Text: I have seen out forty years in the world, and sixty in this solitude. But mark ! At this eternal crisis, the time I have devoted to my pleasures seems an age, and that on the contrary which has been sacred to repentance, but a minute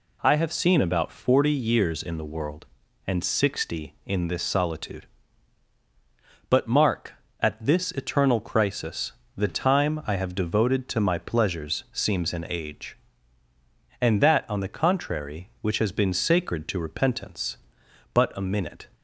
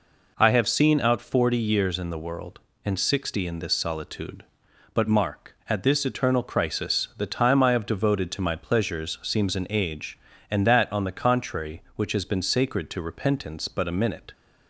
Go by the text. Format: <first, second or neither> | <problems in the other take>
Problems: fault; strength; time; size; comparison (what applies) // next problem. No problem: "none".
second | says "about" for "out"; at 0.8 s